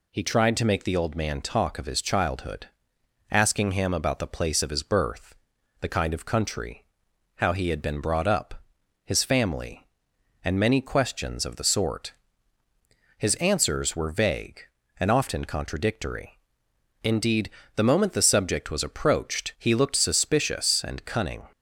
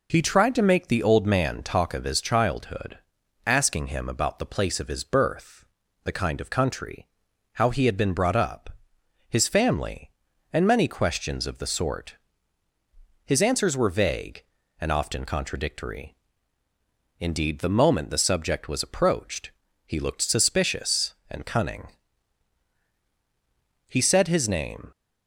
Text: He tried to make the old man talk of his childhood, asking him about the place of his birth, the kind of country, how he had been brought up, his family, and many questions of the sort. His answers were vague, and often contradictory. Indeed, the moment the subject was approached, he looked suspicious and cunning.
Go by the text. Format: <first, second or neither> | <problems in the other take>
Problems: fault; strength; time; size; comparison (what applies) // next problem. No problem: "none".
first | goes on to say "He said his name"; noticeable; from 23.8 s on; 1.0 s long